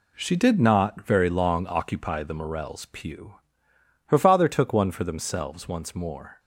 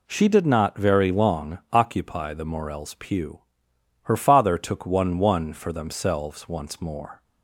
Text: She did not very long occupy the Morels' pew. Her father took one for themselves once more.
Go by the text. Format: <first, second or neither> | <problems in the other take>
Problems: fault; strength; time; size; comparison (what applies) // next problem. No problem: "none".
first | says "one" twice; at 5.1 s